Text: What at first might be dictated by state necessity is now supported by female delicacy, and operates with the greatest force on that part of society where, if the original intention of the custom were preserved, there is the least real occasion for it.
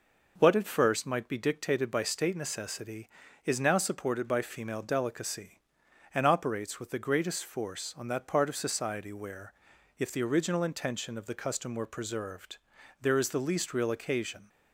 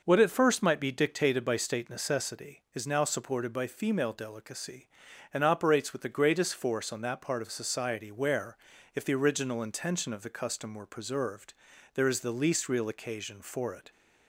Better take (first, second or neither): second